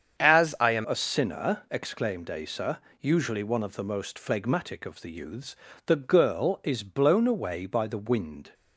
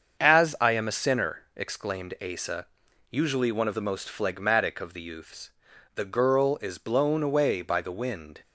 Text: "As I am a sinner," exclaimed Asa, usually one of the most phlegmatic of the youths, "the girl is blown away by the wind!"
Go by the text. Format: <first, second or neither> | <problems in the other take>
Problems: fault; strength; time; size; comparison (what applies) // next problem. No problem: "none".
second | starts louder than the rest; strong; until 1.2 s; 8 dB; also in the second // changes voice at "a"; from 0.8 s on; 7.7 s long